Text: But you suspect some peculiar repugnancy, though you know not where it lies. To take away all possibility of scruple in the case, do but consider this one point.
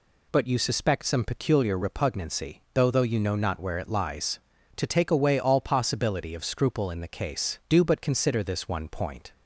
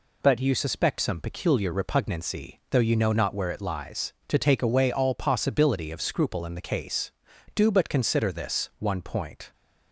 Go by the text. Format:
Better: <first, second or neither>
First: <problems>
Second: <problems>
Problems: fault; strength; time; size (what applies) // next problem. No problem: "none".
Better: second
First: says "though" twice; at 2.9 s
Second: none